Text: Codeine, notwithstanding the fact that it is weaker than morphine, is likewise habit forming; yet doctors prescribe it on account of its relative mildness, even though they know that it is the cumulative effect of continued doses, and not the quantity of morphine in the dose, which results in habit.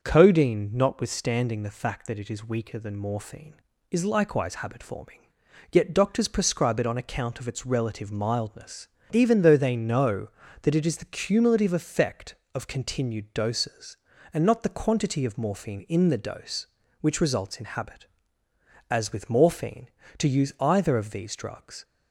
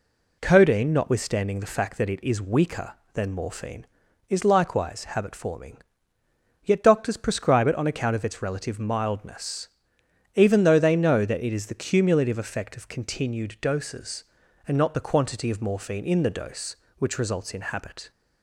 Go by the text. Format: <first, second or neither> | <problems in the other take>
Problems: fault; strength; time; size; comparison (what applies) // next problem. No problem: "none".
second | starts louder than the rest; until 1.0 s; 6.5 dB // goes on to say "As with morphine to use either of these drugs"; strong; from 18.8 s on; 2.9 s long